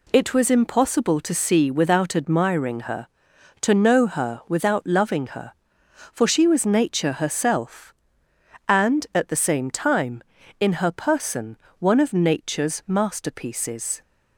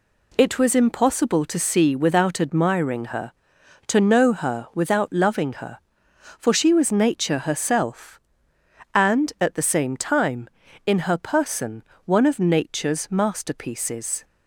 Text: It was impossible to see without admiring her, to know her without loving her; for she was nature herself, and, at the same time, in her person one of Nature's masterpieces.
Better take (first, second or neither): neither